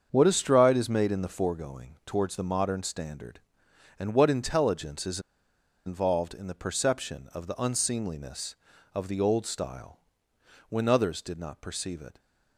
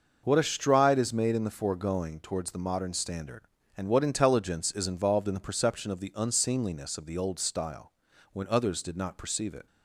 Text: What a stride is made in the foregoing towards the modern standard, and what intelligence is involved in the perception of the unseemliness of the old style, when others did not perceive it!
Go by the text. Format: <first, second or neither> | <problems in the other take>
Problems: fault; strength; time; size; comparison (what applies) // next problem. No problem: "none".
second | starts louder than the rest; strong; until 1.1 s; 7 dB // pauses between "is" and "involved"; noticeable; at 5.2 s; 0.65 s long